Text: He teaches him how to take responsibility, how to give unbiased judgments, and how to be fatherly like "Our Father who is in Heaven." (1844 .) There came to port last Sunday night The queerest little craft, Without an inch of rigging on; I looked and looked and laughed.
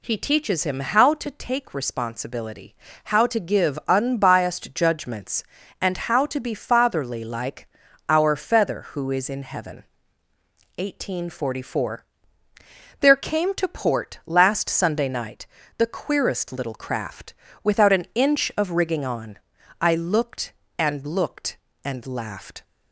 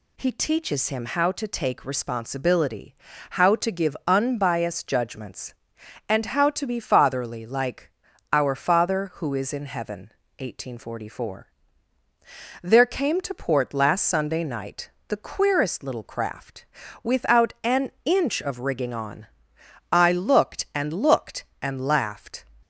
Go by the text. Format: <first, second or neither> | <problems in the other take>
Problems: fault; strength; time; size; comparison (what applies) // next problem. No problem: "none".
second | pauses between "like" and "Our"; at 7.6 s; 0.40 s long; also in the second // says "Feather" for "Father"; at 8.3 s // pauses between "night" and "The"; slight; at 15.4 s; 0.30 s long; slight in the second